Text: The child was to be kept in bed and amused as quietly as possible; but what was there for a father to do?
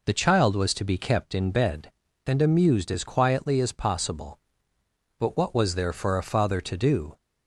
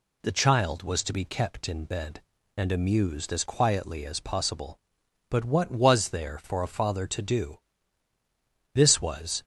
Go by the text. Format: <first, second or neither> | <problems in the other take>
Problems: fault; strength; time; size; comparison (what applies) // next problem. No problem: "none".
first | goes on to say "This was"; noticeable; from 8.7 s on; 0.70 s long